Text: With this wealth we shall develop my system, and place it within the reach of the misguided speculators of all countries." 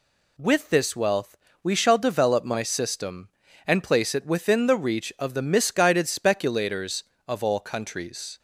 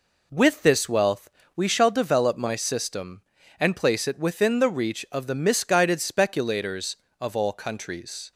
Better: first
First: pauses between "wealth" and "we"; slight; at 1.3 s; 0.24 s long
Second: starts louder than the rest; until 1.6 s; 3.5 dB // pauses between "wealth" and "we"; slight; at 1.3 s; 0.24 s long

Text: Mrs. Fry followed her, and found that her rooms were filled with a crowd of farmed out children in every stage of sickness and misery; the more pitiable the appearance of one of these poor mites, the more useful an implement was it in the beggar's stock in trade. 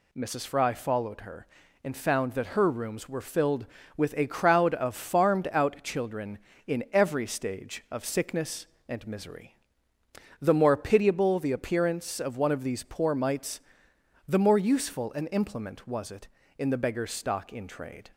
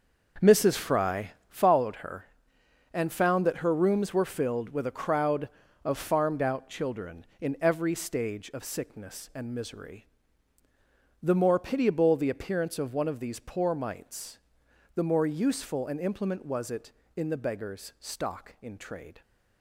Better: first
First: none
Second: starts louder than the rest; noticeable; until 1.6 s; 6 dB // pauses between "Fry" and "followed"; slight; at 1.3 s; 0.18 s long

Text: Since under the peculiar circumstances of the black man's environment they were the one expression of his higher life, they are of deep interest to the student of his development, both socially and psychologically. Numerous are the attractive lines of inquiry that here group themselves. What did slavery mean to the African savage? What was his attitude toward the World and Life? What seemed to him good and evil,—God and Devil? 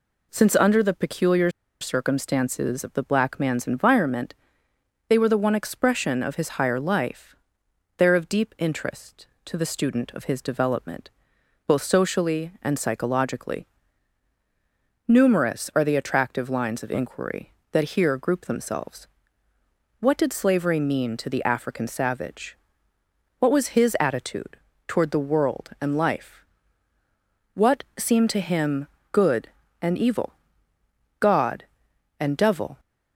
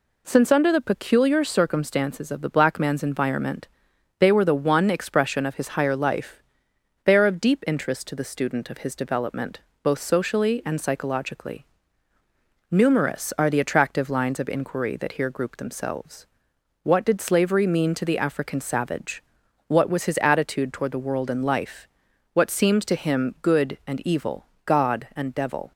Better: second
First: pauses between "peculiar" and "circumstances"; slight; at 1.4 s; 0.31 s long // pauses between "environment" and "they"; noticeable; at 4.3 s; 0.74 s long // pauses between "attitude" and "toward"; slight; at 24.5 s; 0.28 s long // pauses between "What" and "seemed"; slight; at 27.8 s; 0.16 s long // pauses between "him" and "good"; slight; at 28.8 s; 0.26 s long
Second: pauses between "environment" and "they"; noticeable; at 3.6 s; 0.52 s long

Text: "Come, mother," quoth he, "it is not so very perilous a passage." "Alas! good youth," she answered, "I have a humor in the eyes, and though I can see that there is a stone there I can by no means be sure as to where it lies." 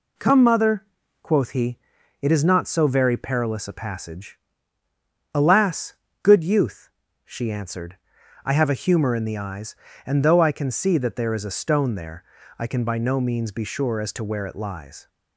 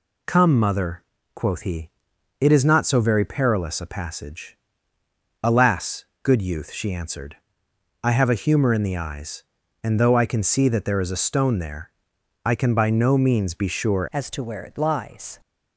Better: first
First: pauses between "there" and "I"; slight; at 12.2 s; 0.34 s long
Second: pauses between "there" and "I"; noticeable; at 11.9 s; 0.52 s long // changes voice at "as"; from 14.1 s on; 1.3 s long

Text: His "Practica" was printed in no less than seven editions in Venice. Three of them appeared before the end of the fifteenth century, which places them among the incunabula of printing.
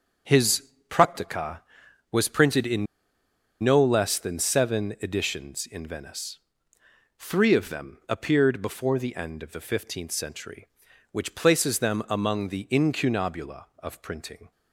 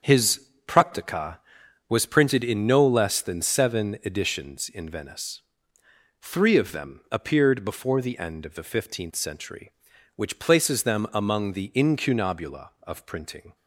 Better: second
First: starts louder than the rest; strong; until 1.4 s; 7 dB // pauses between "His" and "Practica"; slight; at 0.7 s; 0.20 s long // pauses between "in" and "no"; noticeable; at 2.8 s; 0.76 s long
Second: starts louder than the rest; strong; until 1.2 s; 7 dB // pauses between "His" and "Practica"; slight; at 0.4 s; 0.20 s long

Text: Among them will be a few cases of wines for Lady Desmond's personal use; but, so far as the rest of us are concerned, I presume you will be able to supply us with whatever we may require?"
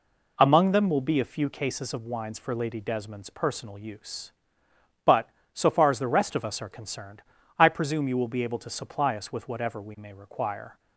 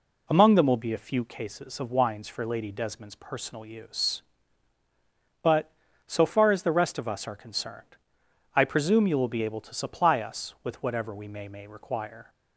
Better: first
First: none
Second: says "may" twice; at 11.4 s

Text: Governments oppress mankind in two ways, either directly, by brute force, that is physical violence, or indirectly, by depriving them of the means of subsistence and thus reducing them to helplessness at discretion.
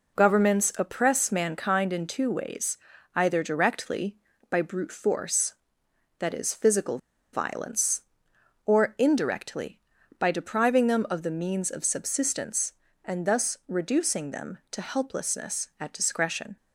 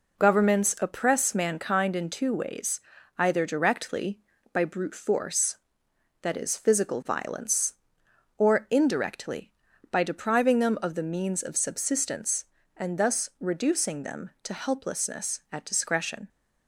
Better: second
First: pauses between "physical" and "violence"; slight; at 6.9 s; 0.36 s long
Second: none

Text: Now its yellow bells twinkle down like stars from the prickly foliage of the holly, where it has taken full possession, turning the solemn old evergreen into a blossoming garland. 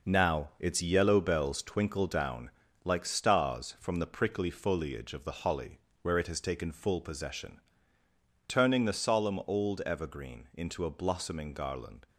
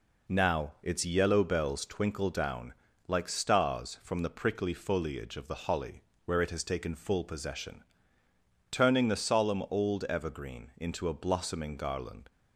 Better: second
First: gets quieter; strong; throughout; 8 dB // pauses between "down" and "like"; slight; at 2.4 s; 0.34 s long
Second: pauses between "down" and "like"; slight; at 2.7 s; 0.34 s long

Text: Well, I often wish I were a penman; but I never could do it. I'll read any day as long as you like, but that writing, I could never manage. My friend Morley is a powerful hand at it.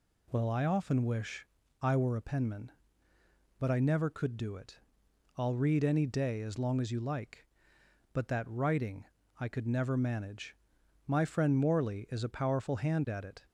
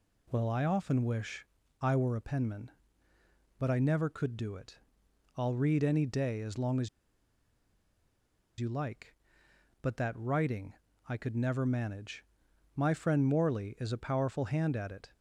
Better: first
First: pauses between "wish" and "I"; slight; at 1.4 s; 0.34 s long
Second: pauses between "wish" and "I"; slight; at 1.4 s; 0.34 s long // pauses between "as" and "you"; strong; at 6.8 s; 1.7 s long

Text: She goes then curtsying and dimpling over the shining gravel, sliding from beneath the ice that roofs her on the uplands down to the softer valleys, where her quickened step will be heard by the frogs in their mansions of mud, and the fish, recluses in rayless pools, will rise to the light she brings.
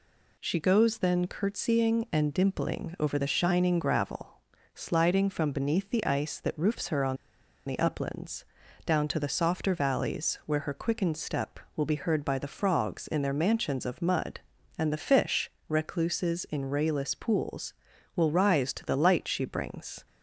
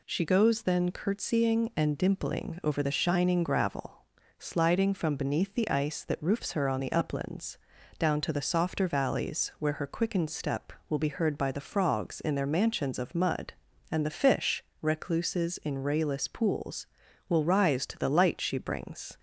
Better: second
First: pauses between "on" and "the"; noticeable; at 7.1 s; 0.50 s long // pauses between "uplands" and "down"; at 8.4 s; 0.40 s long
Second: pauses between "uplands" and "down"; at 7.5 s; 0.40 s long

